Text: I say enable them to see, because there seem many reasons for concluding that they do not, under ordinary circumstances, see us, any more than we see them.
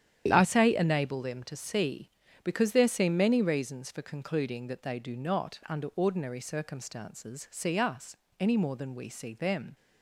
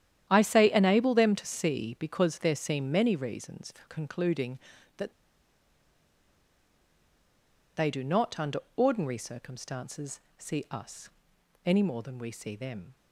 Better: first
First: starts louder than the rest; strong; until 1.3 s; 10 dB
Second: starts louder than the rest; strong; until 1.3 s; 10.5 dB // pauses between "that" and "they"; strong; at 5.1 s; 2.6 s long // pauses between "under" and "ordinary"; slight; at 8.5 s; 0.16 s long

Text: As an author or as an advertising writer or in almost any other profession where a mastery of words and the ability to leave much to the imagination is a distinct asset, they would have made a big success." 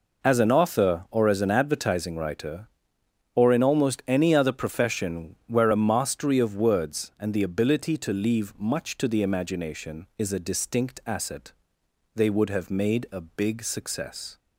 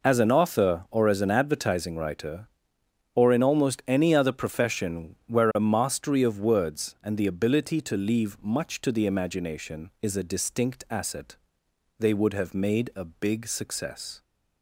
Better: neither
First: none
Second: none

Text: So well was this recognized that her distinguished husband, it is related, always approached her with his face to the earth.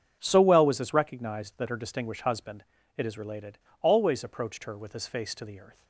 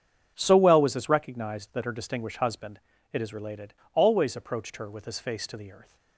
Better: neither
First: starts louder than the rest; strong; until 1.2 s; 7.5 dB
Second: starts louder than the rest; strong; until 1.3 s; 7 dB

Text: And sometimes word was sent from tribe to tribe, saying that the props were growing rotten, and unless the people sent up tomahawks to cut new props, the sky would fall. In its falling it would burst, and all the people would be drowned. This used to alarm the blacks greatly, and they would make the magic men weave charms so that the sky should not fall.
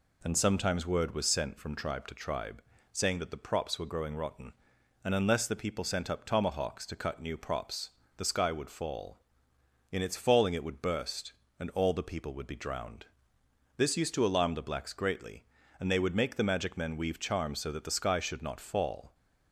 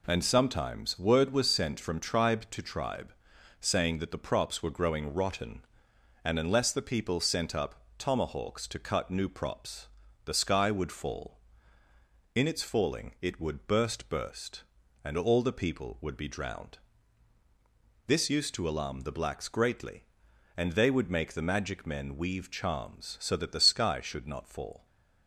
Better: first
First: none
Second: pauses between "up" and "tomahawks"; slight; at 7.8 s; 0.16 s long // says "burst" twice; at 14.1 s

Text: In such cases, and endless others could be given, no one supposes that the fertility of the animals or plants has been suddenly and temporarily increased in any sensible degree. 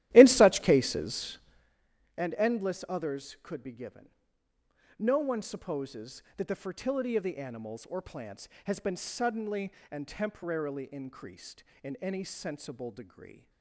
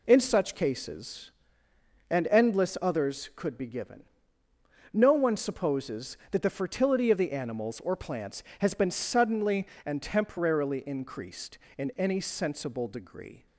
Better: second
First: starts louder than the rest; strong; until 1.8 s; 14 dB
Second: none

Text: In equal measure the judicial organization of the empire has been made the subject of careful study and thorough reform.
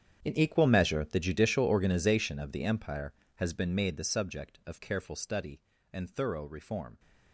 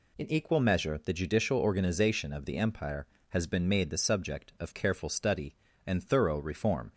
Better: second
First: gets quieter; strong; throughout; 18 dB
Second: none

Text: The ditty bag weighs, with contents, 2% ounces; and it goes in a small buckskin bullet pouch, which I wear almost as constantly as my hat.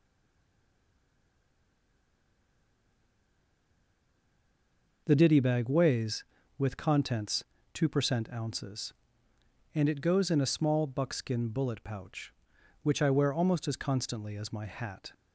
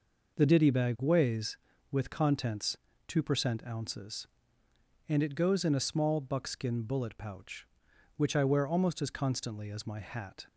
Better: second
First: stays silent before the first word; strong; until 5.0 s; 5.0 s long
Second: none

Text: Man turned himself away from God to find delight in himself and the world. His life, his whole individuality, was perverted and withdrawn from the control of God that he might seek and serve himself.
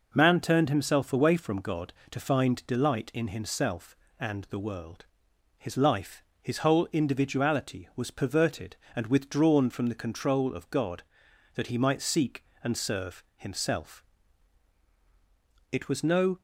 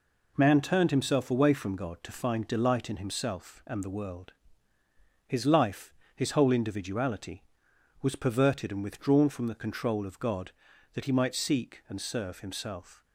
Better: second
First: goes on to say "It was no"; noticeable; from 15.6 s on; 0.72 s long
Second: none

